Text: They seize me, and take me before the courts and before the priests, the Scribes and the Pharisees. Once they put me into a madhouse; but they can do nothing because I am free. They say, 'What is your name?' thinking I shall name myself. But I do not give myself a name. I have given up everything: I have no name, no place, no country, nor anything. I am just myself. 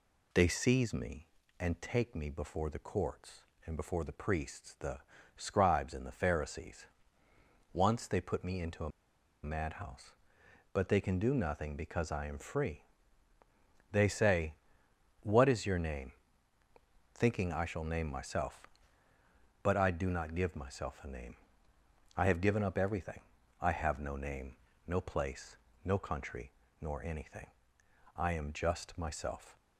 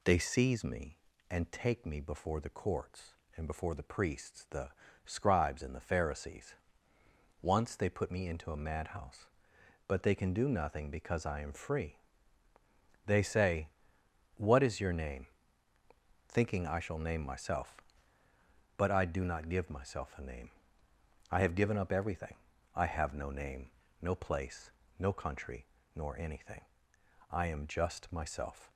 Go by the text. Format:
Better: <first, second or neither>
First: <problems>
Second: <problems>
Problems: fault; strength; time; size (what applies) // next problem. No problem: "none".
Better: second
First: pauses between "the" and "Scribes"; slight; at 4.9 s; 0.36 s long // pauses between "a" and "madhouse"; noticeable; at 8.8 s; 0.54 s long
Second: pauses between "the" and "Scribes"; slight; at 4.6 s; 0.34 s long